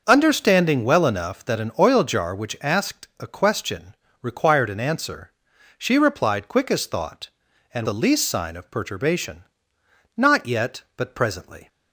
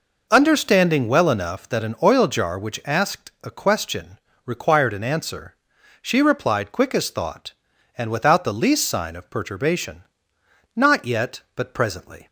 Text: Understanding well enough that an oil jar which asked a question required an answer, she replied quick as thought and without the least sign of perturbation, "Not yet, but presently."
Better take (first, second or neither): second